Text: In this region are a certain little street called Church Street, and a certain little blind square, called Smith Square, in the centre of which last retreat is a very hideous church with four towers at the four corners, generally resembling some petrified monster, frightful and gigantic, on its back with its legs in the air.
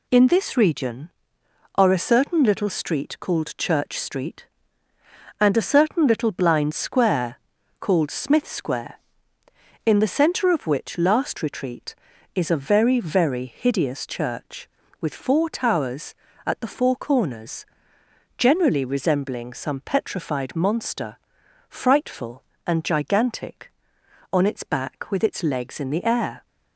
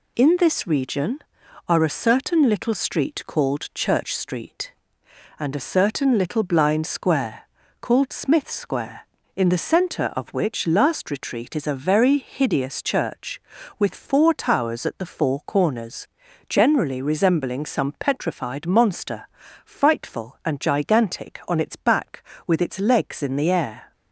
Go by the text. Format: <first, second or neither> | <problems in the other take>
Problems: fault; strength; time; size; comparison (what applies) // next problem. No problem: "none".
second | says "very" twice; at 13.0 s